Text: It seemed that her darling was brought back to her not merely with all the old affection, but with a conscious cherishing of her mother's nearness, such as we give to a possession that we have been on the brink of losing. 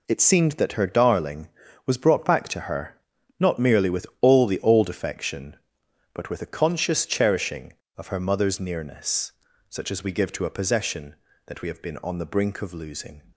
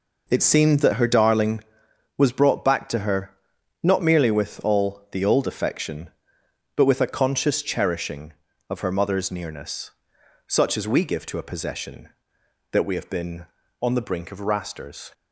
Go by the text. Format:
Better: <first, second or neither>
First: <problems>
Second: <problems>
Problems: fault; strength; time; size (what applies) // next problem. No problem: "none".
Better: first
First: pauses between "her" and "not"; noticeable; at 2.9 s; 0.46 s long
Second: pauses between "her" and "not"; noticeable; at 3.3 s; 0.46 s long // says "rasters" for "losing"; at 14.3 s